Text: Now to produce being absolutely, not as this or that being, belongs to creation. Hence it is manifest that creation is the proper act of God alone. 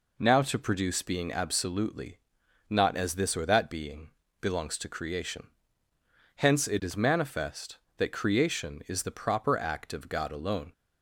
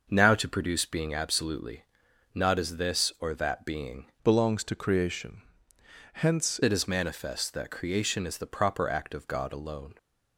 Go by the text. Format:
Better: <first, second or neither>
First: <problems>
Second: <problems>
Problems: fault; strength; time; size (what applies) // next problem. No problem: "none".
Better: first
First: none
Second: changes voice from "belongs" to "Hence"; from 4.2 to 6.6 s; 2.4 s long